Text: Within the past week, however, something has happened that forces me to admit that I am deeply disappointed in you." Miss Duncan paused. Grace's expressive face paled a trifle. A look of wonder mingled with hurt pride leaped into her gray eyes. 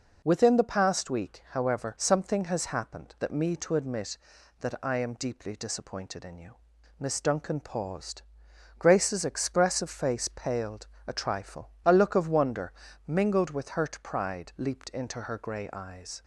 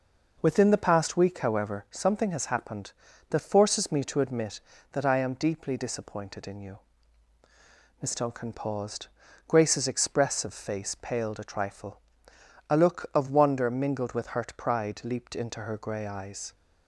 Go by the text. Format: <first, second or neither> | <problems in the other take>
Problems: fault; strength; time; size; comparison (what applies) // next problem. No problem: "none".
second | skips "forces"; at 3.3 s // pauses between "paled" and "a"; slight; at 10.8 s; 0.20 s long // pauses between "wonder" and "mingled"; slight; at 12.7 s; 0.34 s long